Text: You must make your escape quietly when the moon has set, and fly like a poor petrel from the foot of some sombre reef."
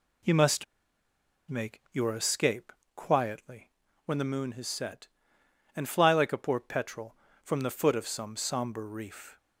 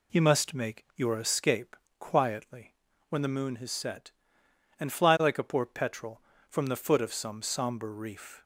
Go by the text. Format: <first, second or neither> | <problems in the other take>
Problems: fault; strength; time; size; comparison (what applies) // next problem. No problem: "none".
second | pauses between "must" and "make"; noticeable; at 0.6 s; 0.84 s long // pauses between "escape" and "quietly"; slight; at 2.7 s; 0.24 s long; slight in the second // pauses between "quietly" and "when"; at 3.6 s; 0.38 s long; also in the second